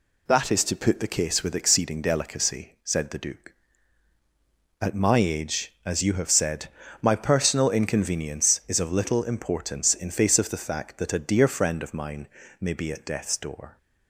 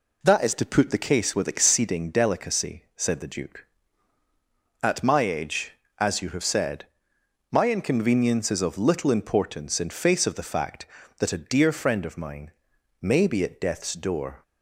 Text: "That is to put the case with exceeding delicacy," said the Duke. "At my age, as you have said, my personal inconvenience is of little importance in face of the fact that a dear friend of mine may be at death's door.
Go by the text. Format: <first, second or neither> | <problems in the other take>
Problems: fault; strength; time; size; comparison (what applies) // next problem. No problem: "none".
first | skips "personal"; at 7.7 s // pauses between "mine" and "may"; noticeable; at 12.5 s; 0.50 s long; slight in the first